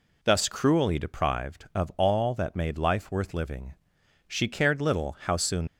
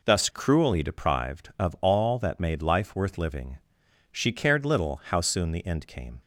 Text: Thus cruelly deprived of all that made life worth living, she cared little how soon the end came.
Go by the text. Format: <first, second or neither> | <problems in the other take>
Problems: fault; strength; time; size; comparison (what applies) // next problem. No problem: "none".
second | stops before "the end came"; at 5.6 s